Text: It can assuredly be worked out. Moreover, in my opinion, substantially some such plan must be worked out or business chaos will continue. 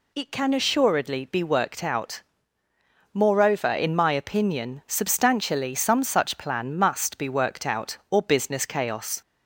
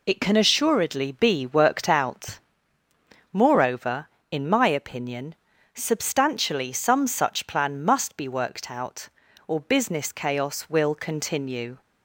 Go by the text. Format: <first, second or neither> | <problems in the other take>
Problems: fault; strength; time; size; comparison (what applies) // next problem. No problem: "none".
second | stops before "will continue"; at 9.2 s